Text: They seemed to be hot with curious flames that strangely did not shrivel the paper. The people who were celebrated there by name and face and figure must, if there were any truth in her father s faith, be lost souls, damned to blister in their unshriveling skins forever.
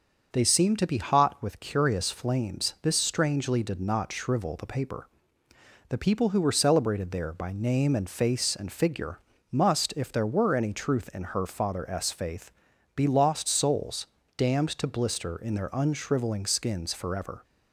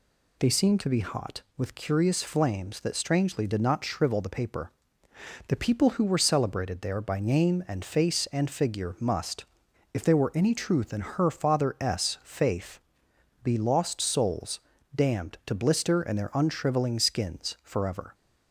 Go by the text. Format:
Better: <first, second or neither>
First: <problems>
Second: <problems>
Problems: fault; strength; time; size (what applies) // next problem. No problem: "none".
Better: second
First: starts louder than the rest; until 1.3 s; 6.5 dB // says "this" for "that"; at 2.8 s // pauses between "figure" and "must"; slight; at 9.1 s; 0.32 s long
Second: none